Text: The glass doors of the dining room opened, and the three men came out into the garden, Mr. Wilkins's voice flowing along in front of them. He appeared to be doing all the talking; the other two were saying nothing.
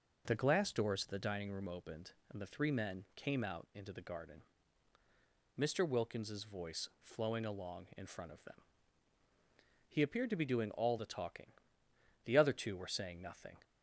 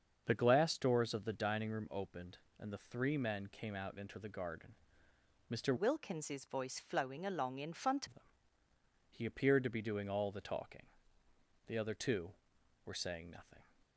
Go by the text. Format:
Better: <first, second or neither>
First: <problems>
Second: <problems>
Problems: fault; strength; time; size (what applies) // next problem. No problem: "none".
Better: first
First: none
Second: starts louder than the rest; until 1.2 s; 7 dB // changes voice from "Wilkins's" to "front"; from 5.7 to 8.0 s; 2.3 s long